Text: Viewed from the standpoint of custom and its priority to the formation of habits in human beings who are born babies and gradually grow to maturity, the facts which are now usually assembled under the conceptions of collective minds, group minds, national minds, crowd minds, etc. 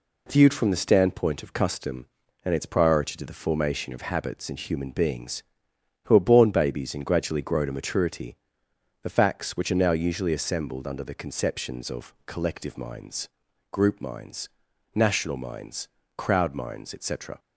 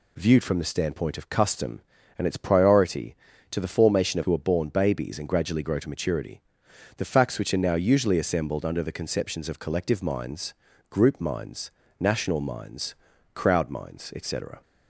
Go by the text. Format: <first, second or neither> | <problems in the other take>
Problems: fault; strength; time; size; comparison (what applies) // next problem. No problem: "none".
first | skips "habits in human beings"; at 4.2 s